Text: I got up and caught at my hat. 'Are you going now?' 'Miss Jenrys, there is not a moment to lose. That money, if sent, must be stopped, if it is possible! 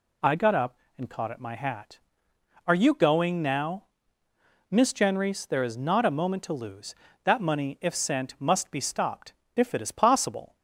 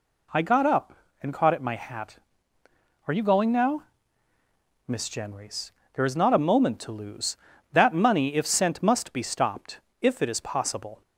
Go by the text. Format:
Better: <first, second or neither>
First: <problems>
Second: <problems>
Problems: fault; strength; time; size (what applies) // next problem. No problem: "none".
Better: neither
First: none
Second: none